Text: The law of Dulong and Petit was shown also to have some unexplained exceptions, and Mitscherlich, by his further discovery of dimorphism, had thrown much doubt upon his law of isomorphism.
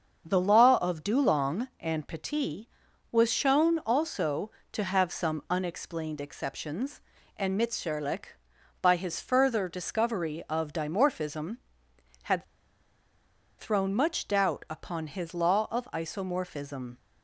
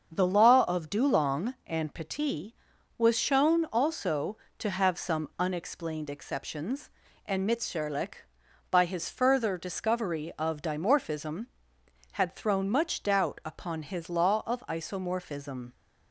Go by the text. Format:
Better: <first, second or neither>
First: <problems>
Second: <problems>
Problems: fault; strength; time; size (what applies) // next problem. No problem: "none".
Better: second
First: starts louder than the rest; until 1.2 s; 6.5 dB // pauses between "had" and "thrown"; at 12.4 s; 1.1 s long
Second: starts louder than the rest; until 1.1 s; 6.5 dB